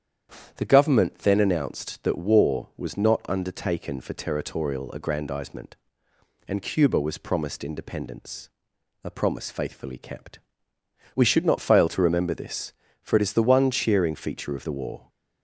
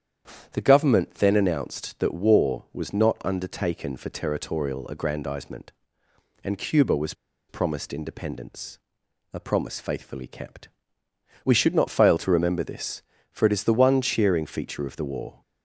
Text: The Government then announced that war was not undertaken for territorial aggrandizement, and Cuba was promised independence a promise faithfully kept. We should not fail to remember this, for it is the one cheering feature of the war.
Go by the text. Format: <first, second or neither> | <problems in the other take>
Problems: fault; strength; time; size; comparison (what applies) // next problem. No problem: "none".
first | starts louder than the rest; strong; until 1.5 s; 9 dB; strong in the first // pauses between "was" and "promised"; slight; at 7.1 s; 0.34 s long // pauses between "independence" and "a"; noticeable; at 8.7 s; 0.54 s long; noticeable in the first